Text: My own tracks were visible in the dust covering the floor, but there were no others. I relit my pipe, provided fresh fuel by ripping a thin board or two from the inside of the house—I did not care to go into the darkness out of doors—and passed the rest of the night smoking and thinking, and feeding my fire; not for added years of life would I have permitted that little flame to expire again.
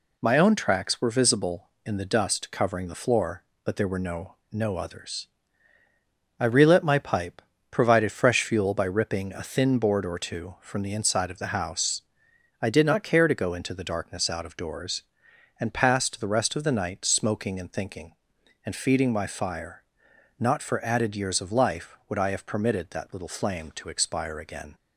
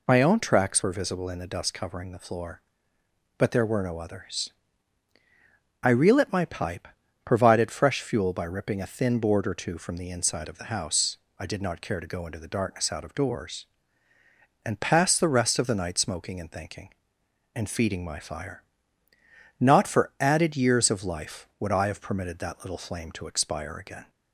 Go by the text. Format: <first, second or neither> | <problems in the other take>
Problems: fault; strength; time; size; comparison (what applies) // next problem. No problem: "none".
second | says "no" twice; at 4.5 s